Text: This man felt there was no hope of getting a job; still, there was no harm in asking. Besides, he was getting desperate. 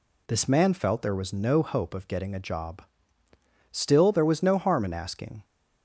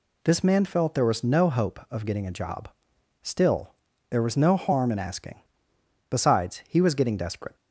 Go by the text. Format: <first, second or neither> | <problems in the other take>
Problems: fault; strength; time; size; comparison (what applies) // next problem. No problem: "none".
second | stops before "Besides he was getting desperate"; at 5.4 s